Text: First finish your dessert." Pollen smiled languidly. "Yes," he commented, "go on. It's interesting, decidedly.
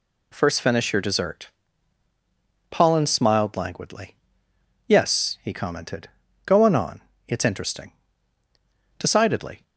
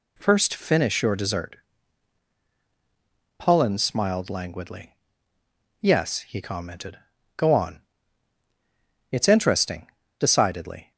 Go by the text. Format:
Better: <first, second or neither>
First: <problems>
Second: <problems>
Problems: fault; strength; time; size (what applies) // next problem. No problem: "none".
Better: second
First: says "on" twice; at 6.7 s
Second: none